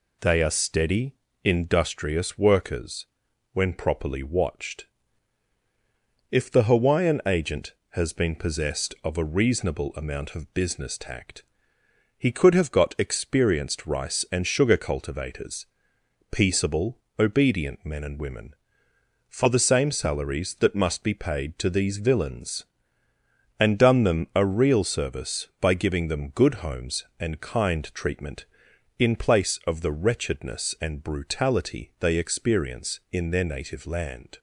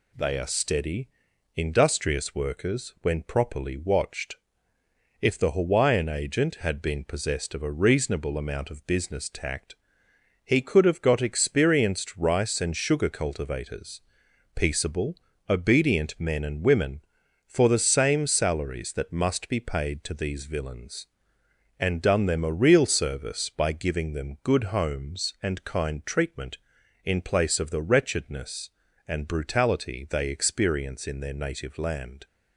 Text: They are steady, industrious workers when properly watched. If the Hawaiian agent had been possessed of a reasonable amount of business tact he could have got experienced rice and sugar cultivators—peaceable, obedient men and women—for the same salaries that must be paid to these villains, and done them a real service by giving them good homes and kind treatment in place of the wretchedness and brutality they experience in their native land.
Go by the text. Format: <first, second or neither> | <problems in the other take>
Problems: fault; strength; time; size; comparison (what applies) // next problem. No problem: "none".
second | pauses between "workers" and "when"; noticeable; at 3.0 s; 0.48 s long // says "has" for "had"; at 7.9 s // pauses between "tact" and "he"; noticeable; at 11.4 s; 0.76 s long; noticeable in the second